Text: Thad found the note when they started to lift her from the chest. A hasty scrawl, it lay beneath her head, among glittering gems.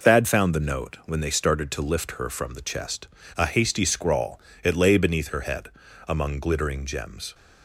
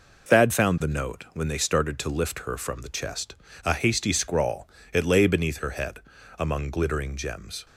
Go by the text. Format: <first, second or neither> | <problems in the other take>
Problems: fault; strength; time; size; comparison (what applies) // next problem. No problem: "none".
neither | none